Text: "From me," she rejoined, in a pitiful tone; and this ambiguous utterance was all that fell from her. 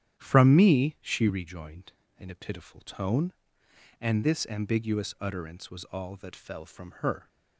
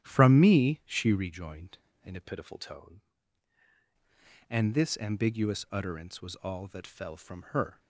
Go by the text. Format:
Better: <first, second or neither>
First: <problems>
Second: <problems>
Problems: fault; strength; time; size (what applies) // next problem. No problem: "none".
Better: first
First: starts louder than the rest; strong; until 1.2 s; 10 dB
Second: starts louder than the rest; strong; until 1.0 s; 10.5 dB // changes voice from "pitiful" to "tone"; from 2.2 to 2.9 s; 0.7 s long